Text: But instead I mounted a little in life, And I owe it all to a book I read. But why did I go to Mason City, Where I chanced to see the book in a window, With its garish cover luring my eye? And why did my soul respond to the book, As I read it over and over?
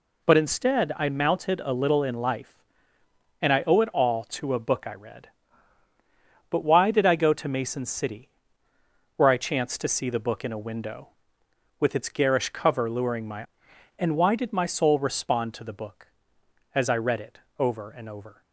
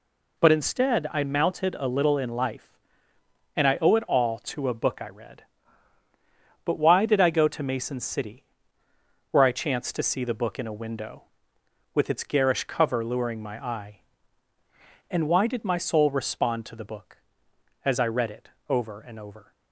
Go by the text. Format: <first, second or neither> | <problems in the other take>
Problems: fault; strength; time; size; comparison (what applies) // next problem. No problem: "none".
second | skips "eye"; at 13.7 s // pauses between "it" and "over"; slight; at 17.3 s; 0.18 s long; slight in the second